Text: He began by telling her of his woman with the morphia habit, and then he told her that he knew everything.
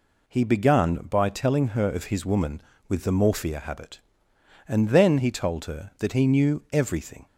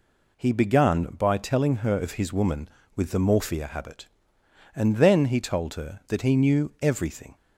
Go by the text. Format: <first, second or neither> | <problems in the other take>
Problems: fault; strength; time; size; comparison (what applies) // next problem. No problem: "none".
neither | none